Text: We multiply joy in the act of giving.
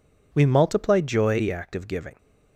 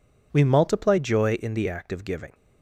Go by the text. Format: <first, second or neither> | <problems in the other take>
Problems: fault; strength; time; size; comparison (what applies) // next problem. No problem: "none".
second | skips "in"; at 1.3 s